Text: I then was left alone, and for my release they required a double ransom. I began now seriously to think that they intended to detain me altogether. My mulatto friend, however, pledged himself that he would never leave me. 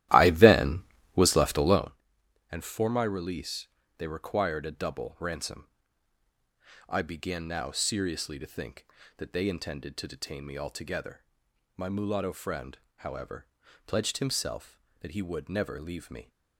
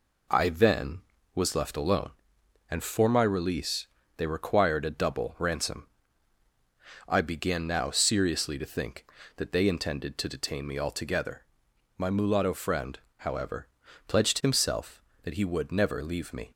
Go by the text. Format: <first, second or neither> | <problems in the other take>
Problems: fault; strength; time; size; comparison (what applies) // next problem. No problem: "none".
second | starts louder than the rest; strong; until 2.0 s; 14 dB // pauses between "release" and "they"; slight; at 3.6 s; 0.30 s long; slight in the second